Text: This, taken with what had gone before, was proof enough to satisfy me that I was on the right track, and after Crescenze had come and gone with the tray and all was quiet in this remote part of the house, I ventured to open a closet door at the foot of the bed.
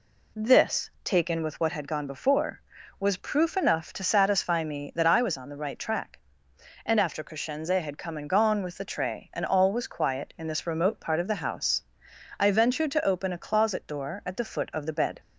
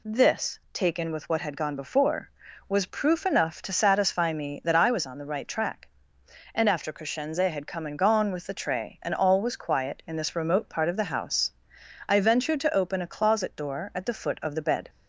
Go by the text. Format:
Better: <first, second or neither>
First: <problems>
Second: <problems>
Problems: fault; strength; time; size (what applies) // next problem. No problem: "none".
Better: second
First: starts louder than the rest; slight; until 1.8 s; 2 dB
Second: none